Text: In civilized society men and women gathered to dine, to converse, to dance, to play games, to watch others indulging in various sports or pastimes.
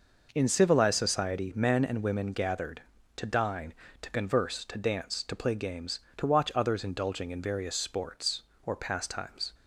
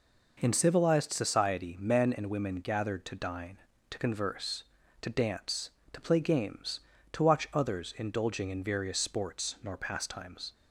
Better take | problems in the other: first | says "nor" for "or"; at 9.6 s

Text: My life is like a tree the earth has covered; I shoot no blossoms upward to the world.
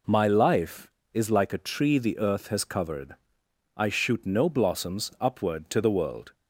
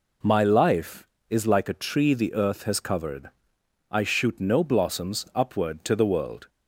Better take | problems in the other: neither | none

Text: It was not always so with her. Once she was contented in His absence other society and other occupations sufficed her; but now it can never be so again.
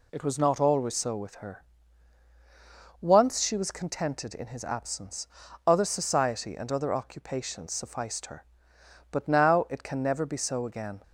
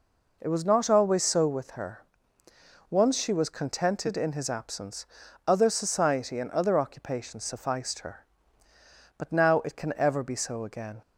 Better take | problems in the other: first | pauses between "absence" and "other"; at 5.0 s; 0.40 s long; also in the first // says "ever" for "never"; at 9.9 s

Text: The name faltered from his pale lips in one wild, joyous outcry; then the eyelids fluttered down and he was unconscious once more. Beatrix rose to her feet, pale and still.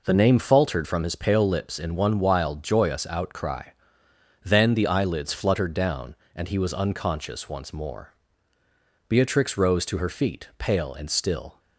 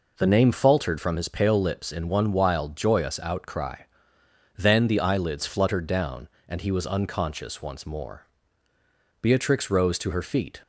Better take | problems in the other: first | stops before "pale and still"; at 10.6 s

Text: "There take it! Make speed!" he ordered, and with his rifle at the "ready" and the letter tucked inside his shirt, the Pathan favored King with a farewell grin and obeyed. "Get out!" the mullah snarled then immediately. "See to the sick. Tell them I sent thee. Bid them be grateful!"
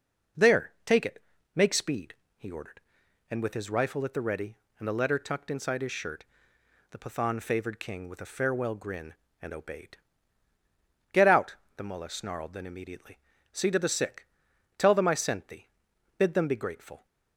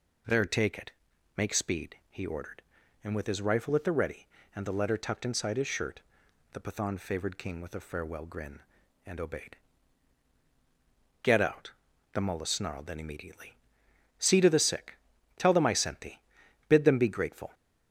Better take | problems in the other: neither | none

